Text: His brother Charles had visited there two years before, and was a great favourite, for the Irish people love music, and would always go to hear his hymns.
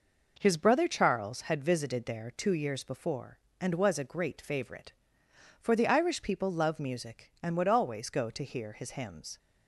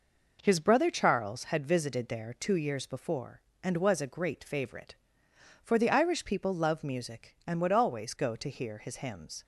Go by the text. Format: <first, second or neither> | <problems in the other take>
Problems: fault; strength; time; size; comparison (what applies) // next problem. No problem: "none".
neither | none